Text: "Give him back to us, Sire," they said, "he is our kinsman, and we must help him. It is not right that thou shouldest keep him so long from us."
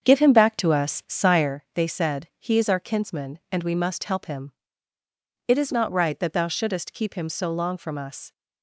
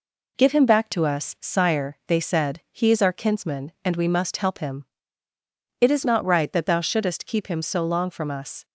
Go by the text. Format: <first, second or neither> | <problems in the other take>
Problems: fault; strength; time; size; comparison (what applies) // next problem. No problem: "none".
second | starts louder than the rest; strong; until 1.6 s; 7.5 dB